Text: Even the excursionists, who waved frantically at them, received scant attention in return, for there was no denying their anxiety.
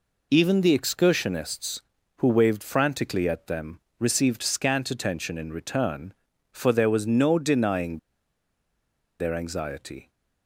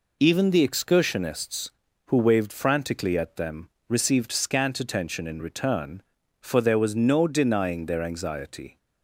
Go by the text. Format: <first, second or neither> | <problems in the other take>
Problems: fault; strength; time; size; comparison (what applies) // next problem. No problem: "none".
second | pauses between "denying" and "their"; at 7.9 s; 1.2 s long